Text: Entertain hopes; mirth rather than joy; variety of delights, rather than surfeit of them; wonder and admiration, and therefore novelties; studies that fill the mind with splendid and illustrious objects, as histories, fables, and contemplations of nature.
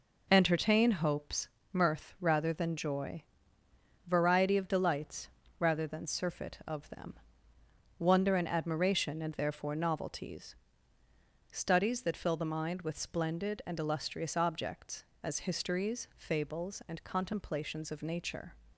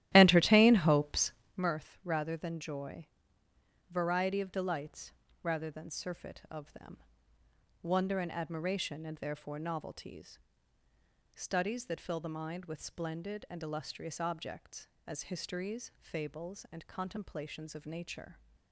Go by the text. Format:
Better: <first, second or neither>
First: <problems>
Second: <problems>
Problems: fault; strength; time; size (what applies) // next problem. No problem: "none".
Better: first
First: none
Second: starts louder than the rest; strong; until 1.7 s; 14 dB